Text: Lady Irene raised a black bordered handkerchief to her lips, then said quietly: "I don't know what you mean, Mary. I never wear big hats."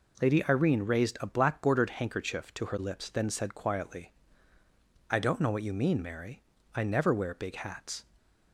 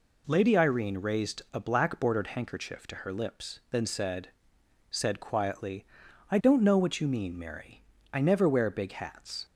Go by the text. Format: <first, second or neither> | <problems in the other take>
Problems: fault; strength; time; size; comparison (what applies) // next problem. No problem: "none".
first | says "said" twice; at 4.8 s